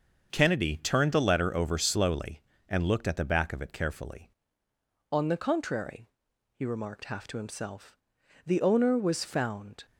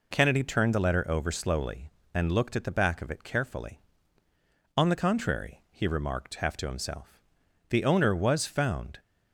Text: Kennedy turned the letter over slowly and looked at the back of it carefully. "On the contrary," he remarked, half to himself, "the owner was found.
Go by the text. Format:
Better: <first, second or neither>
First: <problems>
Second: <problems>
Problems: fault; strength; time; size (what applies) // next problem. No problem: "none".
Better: second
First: starts louder than the rest; until 1.3 s; 6 dB // changes voice at "On"; from 5.1 s on; 4.7 s long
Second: none